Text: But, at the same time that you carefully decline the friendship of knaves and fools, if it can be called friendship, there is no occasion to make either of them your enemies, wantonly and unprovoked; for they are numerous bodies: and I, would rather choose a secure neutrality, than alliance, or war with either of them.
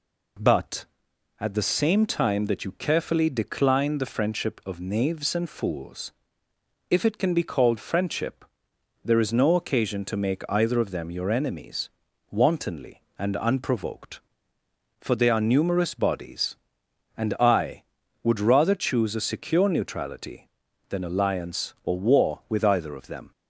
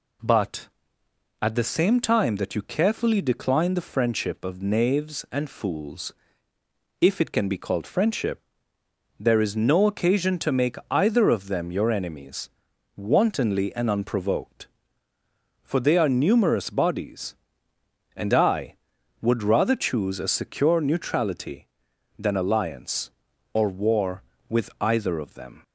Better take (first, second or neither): neither